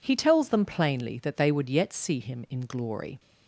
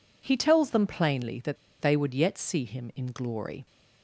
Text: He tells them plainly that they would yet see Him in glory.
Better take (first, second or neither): first